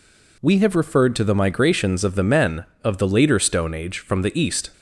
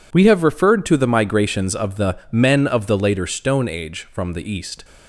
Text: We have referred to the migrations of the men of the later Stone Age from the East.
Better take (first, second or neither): neither